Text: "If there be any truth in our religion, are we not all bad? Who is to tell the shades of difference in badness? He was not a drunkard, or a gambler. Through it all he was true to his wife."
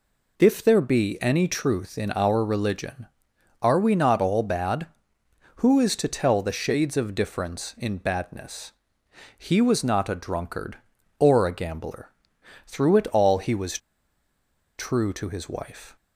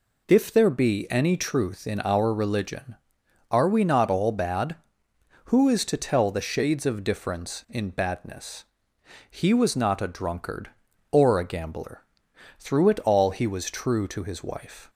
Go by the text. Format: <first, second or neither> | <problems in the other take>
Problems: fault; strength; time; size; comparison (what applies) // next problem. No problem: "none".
second | pauses between "was" and "true"; at 13.7 s; 1.0 s long